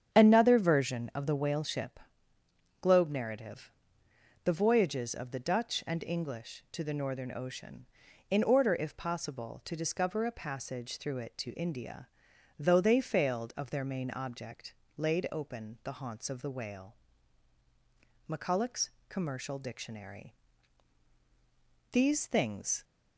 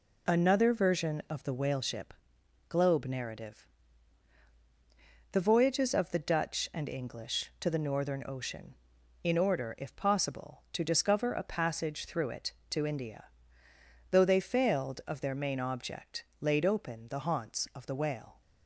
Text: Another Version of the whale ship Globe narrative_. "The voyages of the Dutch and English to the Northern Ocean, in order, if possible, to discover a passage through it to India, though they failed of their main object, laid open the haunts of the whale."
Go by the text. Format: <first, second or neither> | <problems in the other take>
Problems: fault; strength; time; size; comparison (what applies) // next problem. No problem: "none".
second | starts louder than the rest; strong; until 1.1 s; 8.5 dB // pauses between "ship" and "Globe"; noticeable; at 1.9 s; 0.84 s long; noticeable in the second // goes on to say "McCulloch's Commercial Dictionary These things"; strong; from 18.2 s on; 4.5 s long